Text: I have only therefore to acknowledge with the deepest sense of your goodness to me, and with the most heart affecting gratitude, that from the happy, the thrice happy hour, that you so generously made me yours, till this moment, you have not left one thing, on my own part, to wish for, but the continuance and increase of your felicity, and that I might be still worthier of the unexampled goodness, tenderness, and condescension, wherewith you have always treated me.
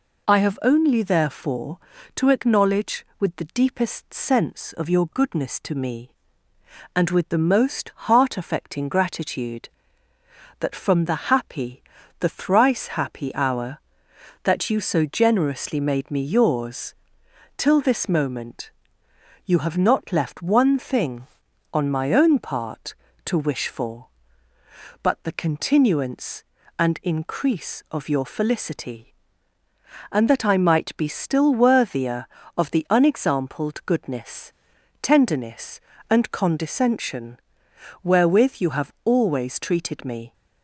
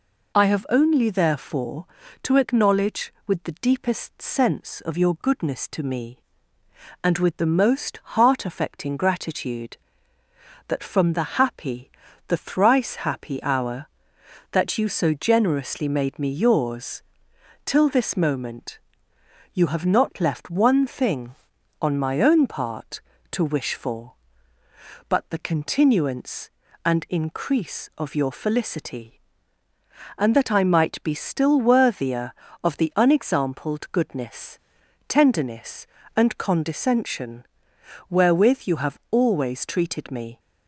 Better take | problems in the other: neither | pauses between "most" and "heart"; slight; the same in both

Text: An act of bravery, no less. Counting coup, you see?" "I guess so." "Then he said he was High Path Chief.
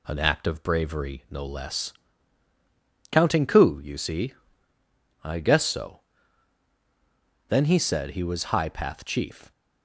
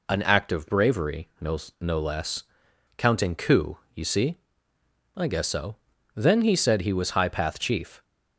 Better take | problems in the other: first | says "no" twice; at 1.8 s

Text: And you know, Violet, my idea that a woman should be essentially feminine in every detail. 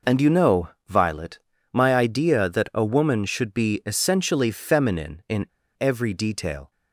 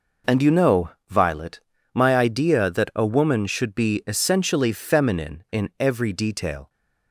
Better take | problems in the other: second | pauses between "in" and "every"; slight; at 5.4 s; 0.34 s long

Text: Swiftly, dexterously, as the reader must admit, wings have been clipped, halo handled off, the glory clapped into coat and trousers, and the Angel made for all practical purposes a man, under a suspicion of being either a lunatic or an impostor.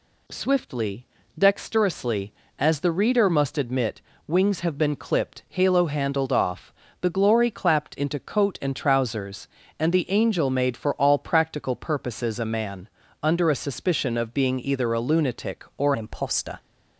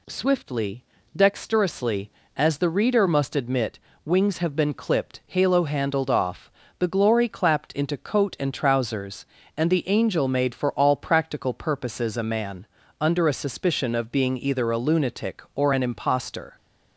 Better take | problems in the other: second | changes voice at "an"; from 15.9 s on; 0.6 s long

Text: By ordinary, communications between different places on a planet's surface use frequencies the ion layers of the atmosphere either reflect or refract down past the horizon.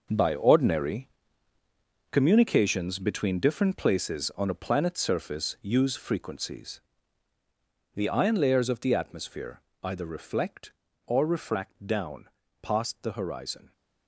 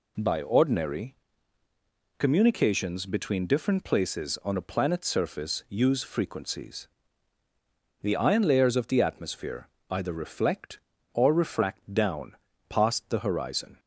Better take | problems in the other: second | gets quieter; strong; throughout; 12 dB // pauses between "frequencies" and "the"; at 6.7 s; 1.1 s long; also in the second // pauses between "atmosphere" and "either"; slight; at 9.5 s; 0.22 s long; slight in the second // pauses between "down" and "past"; slight; at 12.2 s; 0.34 s long; slight in the second

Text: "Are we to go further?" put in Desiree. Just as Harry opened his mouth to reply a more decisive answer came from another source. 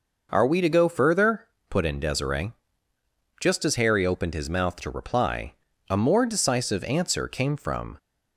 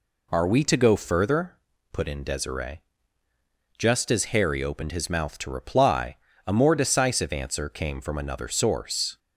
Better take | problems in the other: second | pauses between "reply" and "a"; slight; at 5.5 s; 0.36 s long; slight in the second // stops before "another source"; at 7.9 s

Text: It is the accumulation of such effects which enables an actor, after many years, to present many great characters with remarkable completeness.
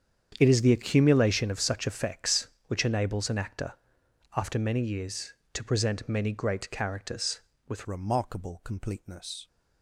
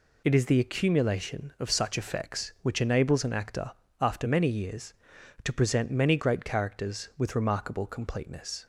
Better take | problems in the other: second | starts louder than the rest; strong; until 1.4 s; 8.5 dB // changes voice at "remarkable"; from 7.8 s on; 1.6 s long

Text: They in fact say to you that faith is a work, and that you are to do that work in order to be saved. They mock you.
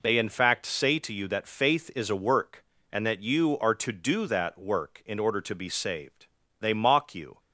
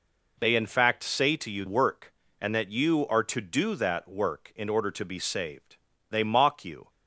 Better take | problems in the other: first | skips "that faith is a"; at 1.6 s

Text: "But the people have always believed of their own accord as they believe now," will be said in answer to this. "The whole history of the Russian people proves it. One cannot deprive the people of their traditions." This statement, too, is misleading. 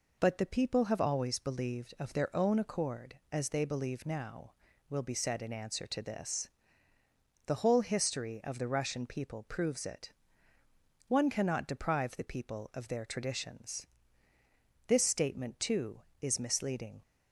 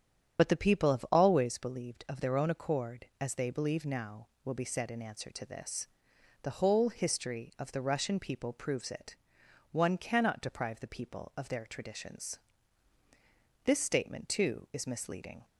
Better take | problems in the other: first | loses the start of "But"; at 0.3 s; 40 ms // starts louder than the rest; strong; until 1.4 s; 8.5 dB

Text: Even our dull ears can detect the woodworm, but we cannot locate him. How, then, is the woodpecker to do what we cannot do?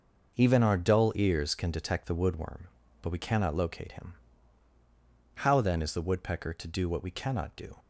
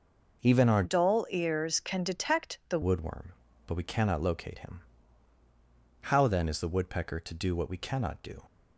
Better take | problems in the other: first | changes voice from "dull" to "the"; from 0.8 to 2.7 s; 1.9 s long

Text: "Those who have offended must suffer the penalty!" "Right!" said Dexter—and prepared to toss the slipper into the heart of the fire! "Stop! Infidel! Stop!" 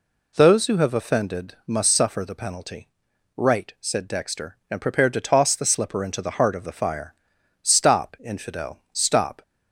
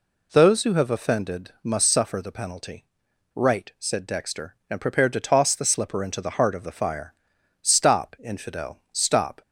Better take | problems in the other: neither | none

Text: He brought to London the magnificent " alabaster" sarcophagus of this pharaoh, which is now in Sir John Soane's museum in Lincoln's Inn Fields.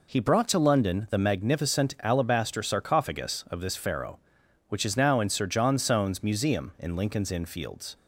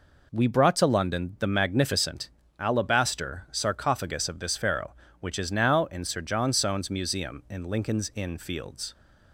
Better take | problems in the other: first | says "We" for "He"; at 0.3 s

